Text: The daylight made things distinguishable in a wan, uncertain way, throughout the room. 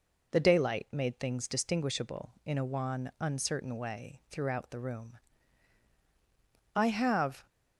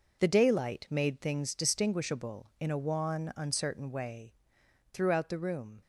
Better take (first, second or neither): second